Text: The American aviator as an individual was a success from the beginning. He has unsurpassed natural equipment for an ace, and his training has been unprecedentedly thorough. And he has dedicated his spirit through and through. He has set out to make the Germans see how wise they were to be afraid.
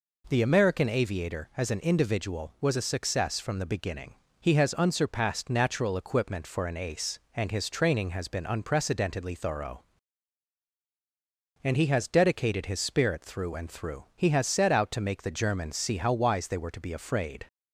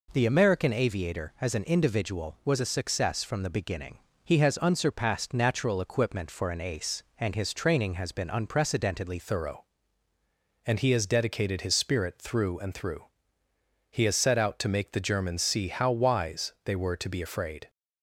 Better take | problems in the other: first | changes voice at "thorough"; from 9.2 s on; 8.4 s long

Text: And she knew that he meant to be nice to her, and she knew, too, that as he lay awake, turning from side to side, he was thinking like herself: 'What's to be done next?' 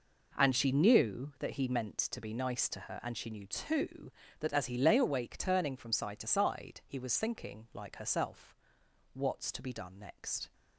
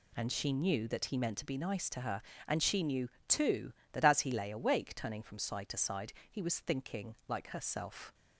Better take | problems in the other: first | stops before "What's to be done next"; at 8.1 s

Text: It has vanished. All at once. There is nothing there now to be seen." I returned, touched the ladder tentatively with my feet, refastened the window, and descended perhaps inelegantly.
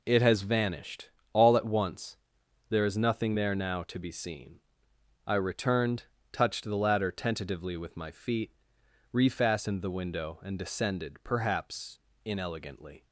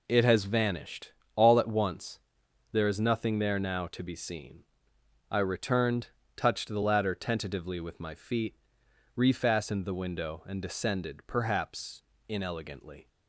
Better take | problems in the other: neither | pauses between "perhaps" and "inelegantly"; slight; the same in both

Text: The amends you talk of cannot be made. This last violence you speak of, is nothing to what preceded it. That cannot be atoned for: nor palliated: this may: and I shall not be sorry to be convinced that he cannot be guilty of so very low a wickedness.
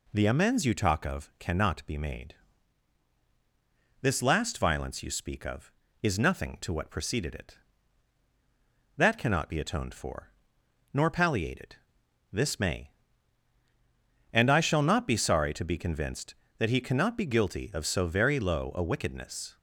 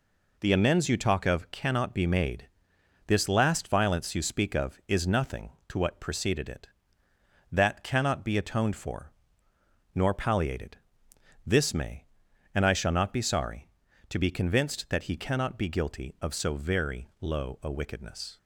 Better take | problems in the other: neither | none

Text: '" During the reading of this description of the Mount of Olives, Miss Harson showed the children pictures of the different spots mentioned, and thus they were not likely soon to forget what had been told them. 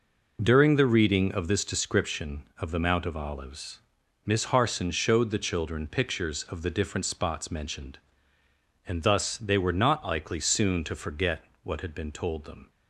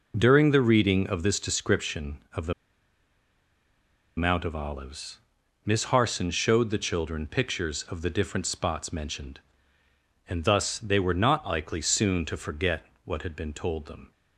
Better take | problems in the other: first | pauses between "the" and "Mount"; strong; at 2.5 s; 1.6 s long // pauses between "forget" and "what"; slight; at 12.8 s; 0.20 s long; slight in the first

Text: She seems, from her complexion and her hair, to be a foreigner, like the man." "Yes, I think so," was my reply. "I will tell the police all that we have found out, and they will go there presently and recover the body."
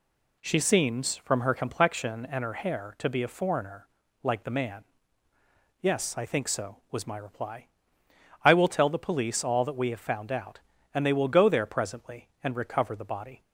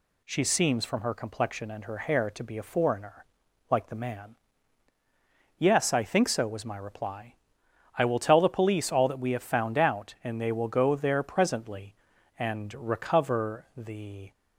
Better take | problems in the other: first | stops before "body"; at 14.3 s

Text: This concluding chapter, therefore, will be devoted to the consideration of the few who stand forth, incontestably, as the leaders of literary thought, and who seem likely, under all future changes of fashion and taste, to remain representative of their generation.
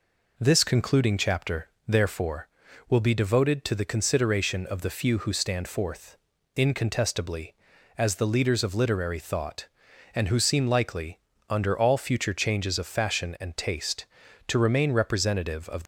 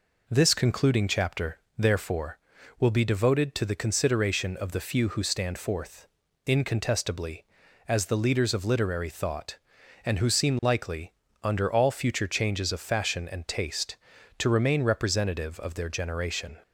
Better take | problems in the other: second | stops before "their generation"; at 15.8 s

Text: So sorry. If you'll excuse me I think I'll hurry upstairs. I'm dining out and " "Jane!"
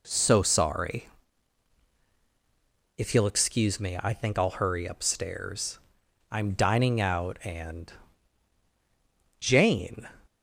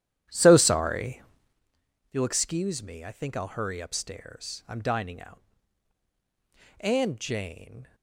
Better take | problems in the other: first | starts louder than the rest; strong; until 1.6 s; 11 dB

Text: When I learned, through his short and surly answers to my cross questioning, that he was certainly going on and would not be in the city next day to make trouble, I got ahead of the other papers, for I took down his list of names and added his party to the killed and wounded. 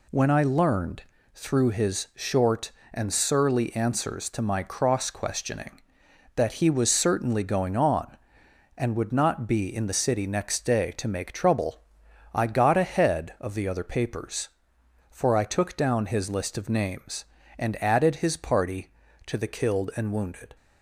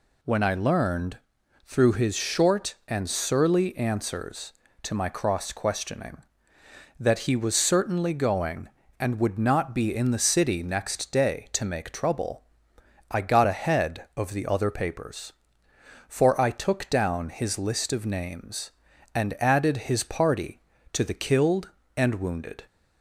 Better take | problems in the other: first | skips "on"; at 8.8 s

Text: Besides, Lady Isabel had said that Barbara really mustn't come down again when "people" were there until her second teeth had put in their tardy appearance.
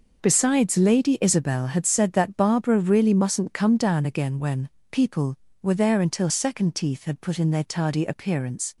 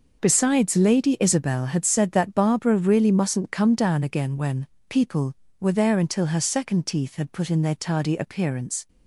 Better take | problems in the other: second | pauses between "when" and "people"; slight; at 4.6 s; 0.24 s long; slight in the second // skips "her"; at 6.2 s

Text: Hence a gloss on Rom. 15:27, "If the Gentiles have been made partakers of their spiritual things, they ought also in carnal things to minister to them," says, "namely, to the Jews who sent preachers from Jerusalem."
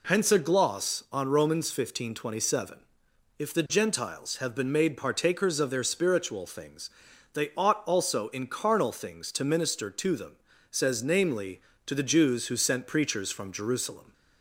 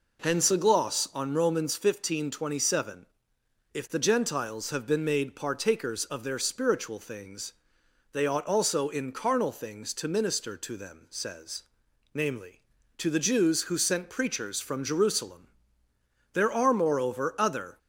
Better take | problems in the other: first | goes on to say "There are moreover other"; from 16.3 s on; 1.4 s long

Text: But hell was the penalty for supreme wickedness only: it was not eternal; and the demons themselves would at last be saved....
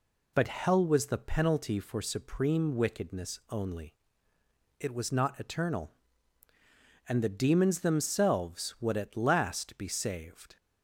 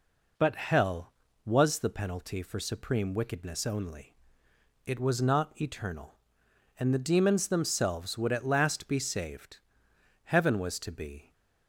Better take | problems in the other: first | goes on to say "Heaven was to be"; noticeable; from 10.2 s on; 1.0 s long

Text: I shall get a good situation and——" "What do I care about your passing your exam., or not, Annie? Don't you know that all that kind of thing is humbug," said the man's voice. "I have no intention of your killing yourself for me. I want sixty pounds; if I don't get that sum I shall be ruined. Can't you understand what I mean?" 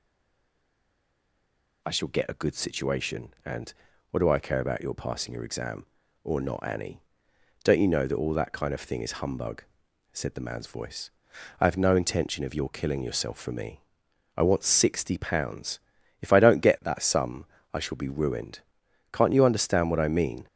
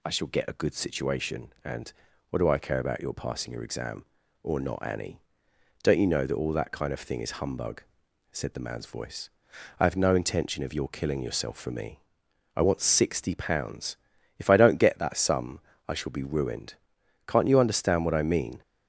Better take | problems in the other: second | stays silent before the first word; noticeable; until 1.8 s; 1.8 s long // pauses between "sum" and "I"; slight; at 17.4 s; 0.30 s long; slight in the second

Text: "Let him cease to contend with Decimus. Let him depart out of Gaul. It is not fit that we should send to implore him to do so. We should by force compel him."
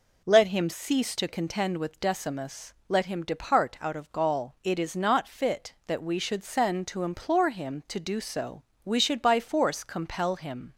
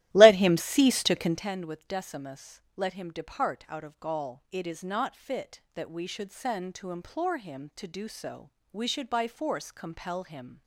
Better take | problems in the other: first | starts louder than the rest; strong; until 1.5 s; 15 dB

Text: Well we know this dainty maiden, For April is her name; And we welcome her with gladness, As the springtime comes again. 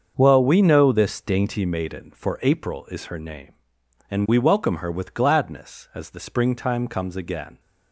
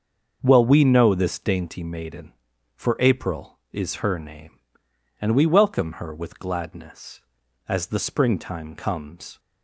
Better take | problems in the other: first | starts louder than the rest; until 1.4 s; 6.5 dB; also in the first // stops before "again"; at 9.3 s

